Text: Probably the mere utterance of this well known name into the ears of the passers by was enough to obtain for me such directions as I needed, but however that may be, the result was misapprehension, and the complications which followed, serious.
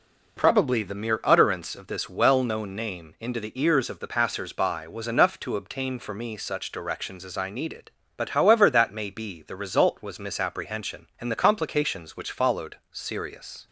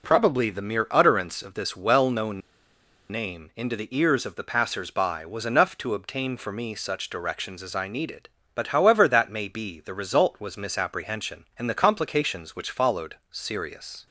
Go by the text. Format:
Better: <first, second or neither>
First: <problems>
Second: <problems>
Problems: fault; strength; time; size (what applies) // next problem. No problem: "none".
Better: first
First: none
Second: pauses between "known" and "name"; noticeable; at 2.4 s; 0.71 s long